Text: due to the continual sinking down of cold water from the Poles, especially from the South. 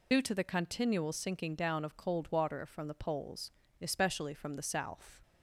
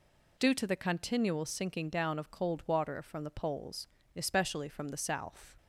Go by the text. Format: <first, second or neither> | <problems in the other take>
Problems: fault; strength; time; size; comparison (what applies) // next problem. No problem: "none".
second | loses the start of "due"; at 0.1 s; 40 ms